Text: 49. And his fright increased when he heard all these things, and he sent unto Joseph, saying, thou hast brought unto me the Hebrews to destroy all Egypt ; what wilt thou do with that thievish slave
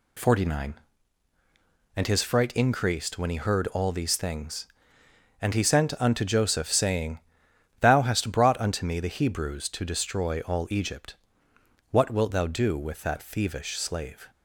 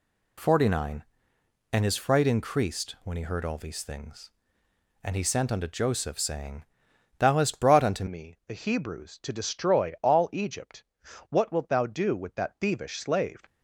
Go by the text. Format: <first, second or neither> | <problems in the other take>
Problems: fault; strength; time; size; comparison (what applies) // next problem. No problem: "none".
first | changes voice at "me"; from 8.0 s on; 5.4 s long